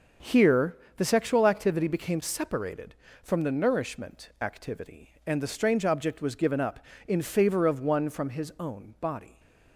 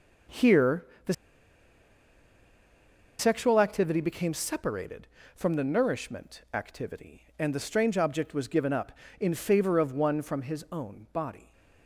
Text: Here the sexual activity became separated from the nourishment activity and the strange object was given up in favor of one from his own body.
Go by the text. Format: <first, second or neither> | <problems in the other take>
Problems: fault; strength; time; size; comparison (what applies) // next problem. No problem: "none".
first | starts louder than the rest; until 3.5 s; 6 dB // pauses between "Here" and "the"; slight; at 0.8 s; 0.20 s long; slight in the first // pauses between "the" and "sexual"; strong; at 1.1 s; 2.0 s long